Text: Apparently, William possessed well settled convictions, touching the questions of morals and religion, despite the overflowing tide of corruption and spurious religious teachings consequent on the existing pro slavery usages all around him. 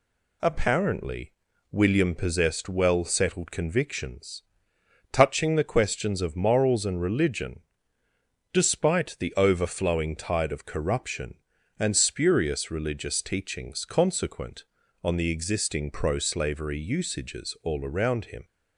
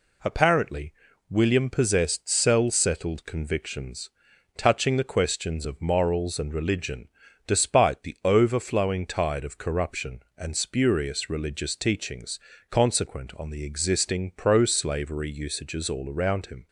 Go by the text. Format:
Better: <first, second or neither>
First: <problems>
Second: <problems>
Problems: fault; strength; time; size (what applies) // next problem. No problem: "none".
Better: first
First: none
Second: says "cell" for "well"; at 2.2 s // pauses between "teachings" and "consequent"; slight; at 12.3 s; 0.30 s long